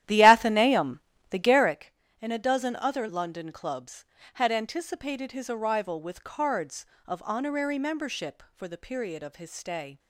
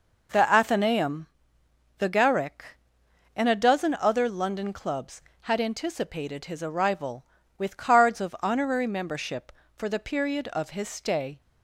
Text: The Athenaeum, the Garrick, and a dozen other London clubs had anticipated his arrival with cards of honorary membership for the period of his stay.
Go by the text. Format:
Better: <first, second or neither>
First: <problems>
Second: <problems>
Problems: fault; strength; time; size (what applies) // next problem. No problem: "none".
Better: second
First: starts louder than the rest; strong; until 1.8 s; 12.5 dB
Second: none